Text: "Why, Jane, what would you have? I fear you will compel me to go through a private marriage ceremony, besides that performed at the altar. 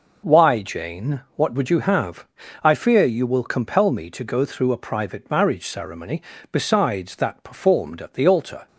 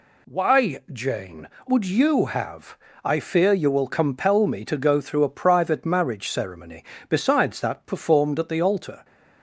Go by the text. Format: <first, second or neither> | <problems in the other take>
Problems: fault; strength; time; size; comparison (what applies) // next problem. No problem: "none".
first | skips "what"; at 1.5 s